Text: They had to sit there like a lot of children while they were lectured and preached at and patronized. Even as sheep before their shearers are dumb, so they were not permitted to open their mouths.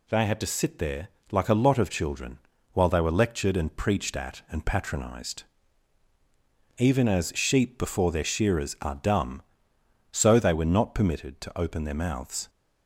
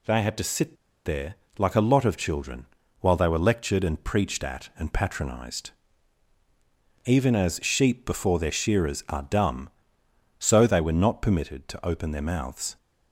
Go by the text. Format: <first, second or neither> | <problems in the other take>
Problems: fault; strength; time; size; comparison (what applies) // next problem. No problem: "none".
first | pauses between "sit" and "there"; slight; at 0.7 s; 0.30 s long // pauses between "there" and "like"; slight; at 1.3 s; 0.24 s long; slight in the first // pauses between "children" and "while"; slight; at 2.6 s; 0.34 s long; slight in the first